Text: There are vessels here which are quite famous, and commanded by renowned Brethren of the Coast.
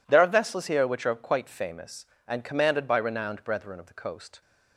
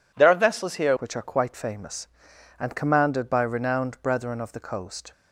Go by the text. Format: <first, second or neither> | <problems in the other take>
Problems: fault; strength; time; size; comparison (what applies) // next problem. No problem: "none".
first | changes voice at "which"; from 0.9 s on; 4.2 s long